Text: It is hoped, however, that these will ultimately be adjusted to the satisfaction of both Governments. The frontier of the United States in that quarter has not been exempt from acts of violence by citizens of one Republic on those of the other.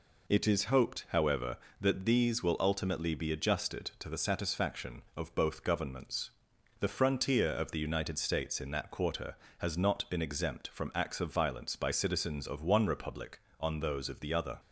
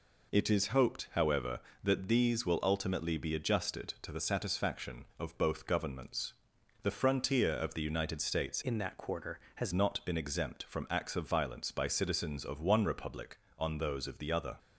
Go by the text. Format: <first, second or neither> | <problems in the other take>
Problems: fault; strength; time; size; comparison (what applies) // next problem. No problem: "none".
first | changes voice from "in" to "has"; from 8.6 to 9.7 s; 1.1 s long